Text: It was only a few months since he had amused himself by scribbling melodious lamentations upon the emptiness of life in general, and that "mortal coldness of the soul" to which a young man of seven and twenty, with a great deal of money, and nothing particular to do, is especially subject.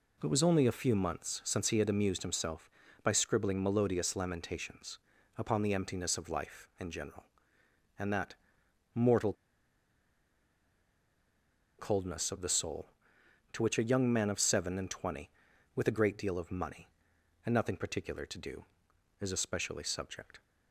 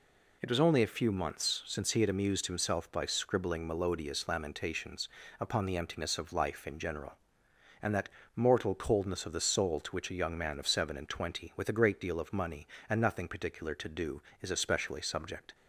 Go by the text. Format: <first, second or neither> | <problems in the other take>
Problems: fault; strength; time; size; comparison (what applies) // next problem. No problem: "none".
second | pauses between "lamentations" and "upon"; at 4.9 s; 0.38 s long; slight in the second // pauses between "that" and "mortal"; noticeable; at 8.3 s; 0.58 s long; slight in the second // pauses between "mortal" and "coldness"; strong; at 9.3 s; 2.4 s long